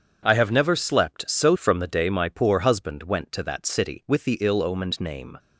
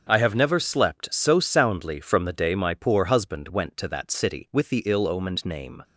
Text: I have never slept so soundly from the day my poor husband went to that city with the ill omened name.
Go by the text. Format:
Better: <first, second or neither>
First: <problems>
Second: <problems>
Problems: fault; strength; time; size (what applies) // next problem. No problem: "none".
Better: second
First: starts louder than the rest; strong; until 1.2 s; 7.5 dB // skips "soundly"; at 1.5 s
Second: starts louder than the rest; until 1.1 s; 6.5 dB